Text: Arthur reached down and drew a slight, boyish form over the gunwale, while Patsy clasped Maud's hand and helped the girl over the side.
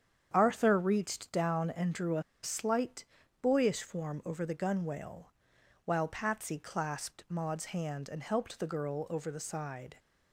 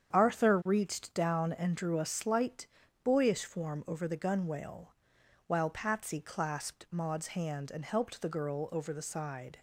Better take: second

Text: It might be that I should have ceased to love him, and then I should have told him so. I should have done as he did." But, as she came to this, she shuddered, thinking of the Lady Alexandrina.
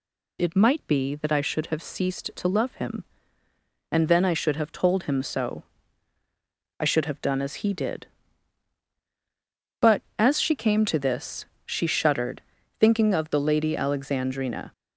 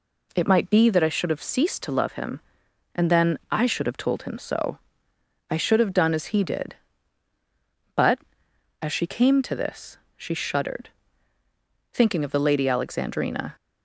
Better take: neither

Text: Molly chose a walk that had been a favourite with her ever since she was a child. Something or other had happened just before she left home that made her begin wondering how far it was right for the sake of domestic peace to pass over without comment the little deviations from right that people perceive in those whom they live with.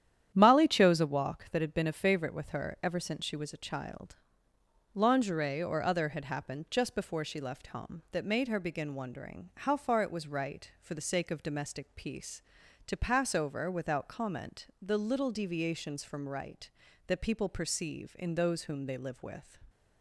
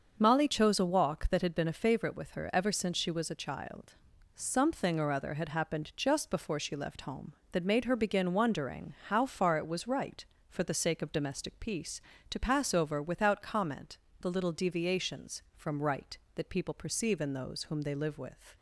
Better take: second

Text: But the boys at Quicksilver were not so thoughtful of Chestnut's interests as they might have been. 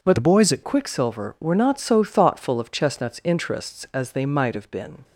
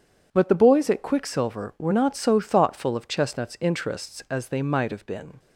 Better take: second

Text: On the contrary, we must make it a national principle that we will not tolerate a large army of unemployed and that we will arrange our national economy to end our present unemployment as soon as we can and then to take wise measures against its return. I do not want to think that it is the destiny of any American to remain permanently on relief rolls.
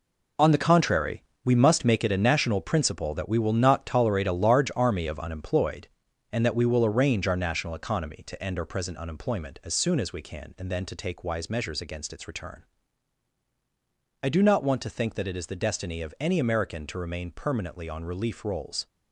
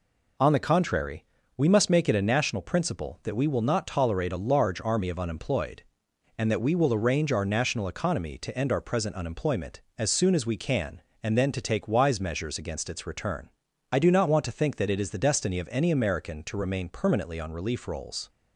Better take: second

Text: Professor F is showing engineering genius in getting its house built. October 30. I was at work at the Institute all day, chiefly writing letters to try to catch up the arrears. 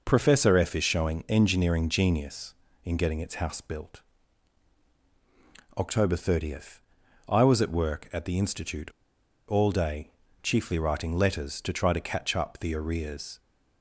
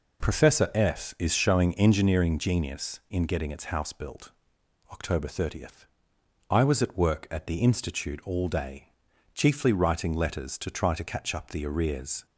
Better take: second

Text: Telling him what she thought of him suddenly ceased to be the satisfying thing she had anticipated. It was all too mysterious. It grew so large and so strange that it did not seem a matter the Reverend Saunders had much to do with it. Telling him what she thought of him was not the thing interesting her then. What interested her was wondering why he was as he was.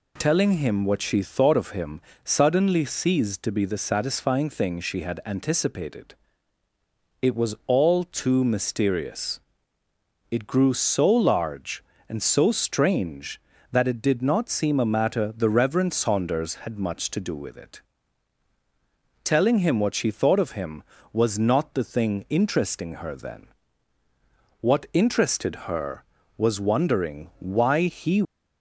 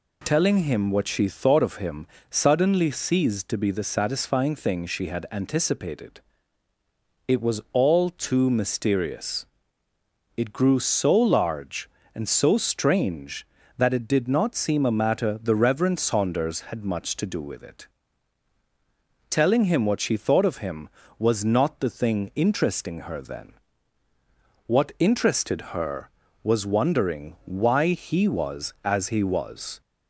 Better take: second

